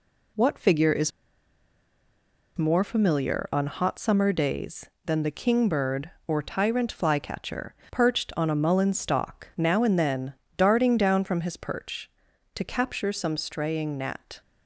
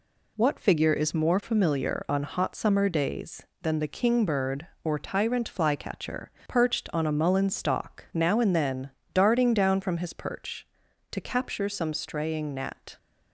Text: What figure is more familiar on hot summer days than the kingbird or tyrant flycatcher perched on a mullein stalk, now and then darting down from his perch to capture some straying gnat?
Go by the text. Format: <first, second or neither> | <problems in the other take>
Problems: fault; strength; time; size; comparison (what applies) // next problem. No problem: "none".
second | pauses between "is" and "more"; strong; at 1.1 s; 1.4 s long // pauses between "flycatcher" and "perched"; slight; at 7.7 s; 0.16 s long; slight in the second // pauses between "then" and "darting"; slight; at 10.3 s; 0.24 s long; slight in the second